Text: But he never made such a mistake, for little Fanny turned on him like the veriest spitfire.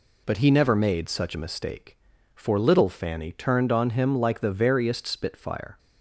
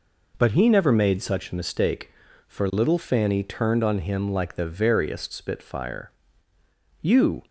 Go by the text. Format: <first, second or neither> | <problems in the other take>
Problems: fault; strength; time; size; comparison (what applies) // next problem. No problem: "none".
first | goes on to say "You"; slight; from 6.9 s on; 0.42 s long